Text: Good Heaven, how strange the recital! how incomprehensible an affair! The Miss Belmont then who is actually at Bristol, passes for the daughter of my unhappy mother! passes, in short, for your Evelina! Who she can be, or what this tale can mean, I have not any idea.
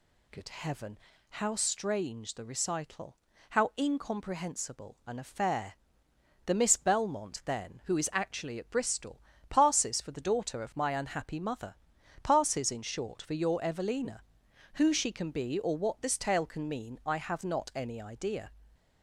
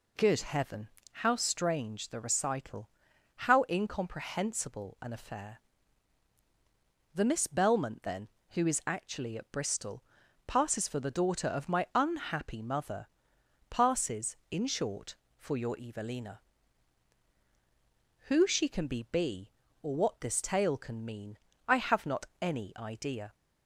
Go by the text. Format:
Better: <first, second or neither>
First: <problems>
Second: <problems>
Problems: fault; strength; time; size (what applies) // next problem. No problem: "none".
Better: first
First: none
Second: says "be" twice; at 19.1 s